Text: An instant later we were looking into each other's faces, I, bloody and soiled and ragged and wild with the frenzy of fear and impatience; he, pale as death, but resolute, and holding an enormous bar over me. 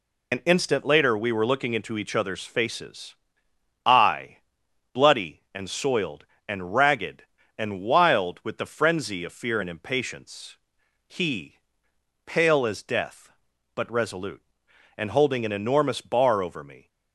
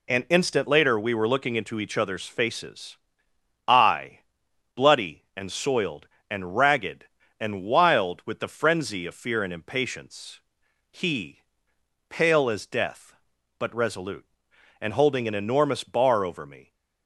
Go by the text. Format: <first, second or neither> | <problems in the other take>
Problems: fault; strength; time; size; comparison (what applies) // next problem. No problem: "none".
second | loses the start of "An"; at 0.3 s; 75 ms